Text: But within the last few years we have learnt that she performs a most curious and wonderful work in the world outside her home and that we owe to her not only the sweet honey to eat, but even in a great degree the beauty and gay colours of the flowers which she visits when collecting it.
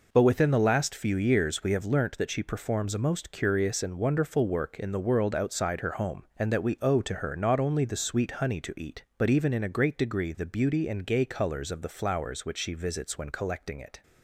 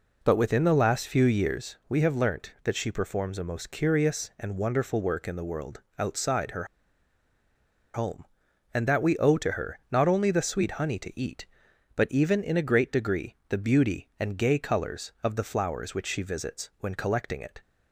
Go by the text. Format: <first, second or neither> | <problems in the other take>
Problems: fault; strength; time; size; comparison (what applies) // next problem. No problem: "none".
first | pauses between "world" and "outside"; slight; at 5.8 s; 0.18 s long // pauses between "her" and "home"; strong; at 6.6 s; 1.2 s long